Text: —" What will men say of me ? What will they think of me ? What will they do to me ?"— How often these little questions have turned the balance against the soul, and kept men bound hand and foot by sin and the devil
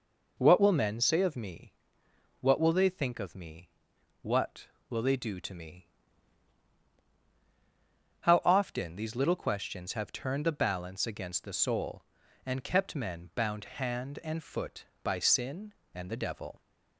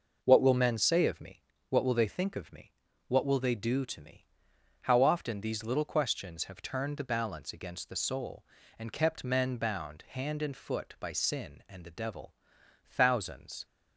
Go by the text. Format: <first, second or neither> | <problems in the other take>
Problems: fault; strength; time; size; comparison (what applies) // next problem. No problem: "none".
first | goes on to say "Thousands"; noticeable; from 12.8 s on; 0.78 s long